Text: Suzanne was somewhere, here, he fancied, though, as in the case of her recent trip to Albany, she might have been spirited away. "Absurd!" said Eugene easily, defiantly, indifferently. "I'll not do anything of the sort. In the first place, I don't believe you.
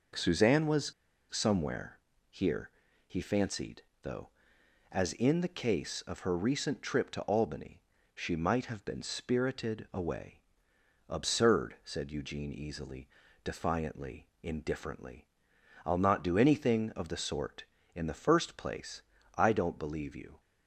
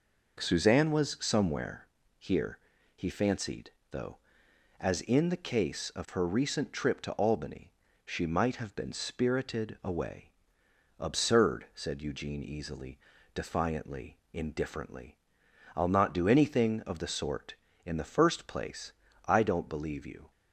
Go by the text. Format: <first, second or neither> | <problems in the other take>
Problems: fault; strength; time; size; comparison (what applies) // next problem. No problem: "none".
second | pauses between "was" and "somewhere"; at 0.9 s; 0.40 s long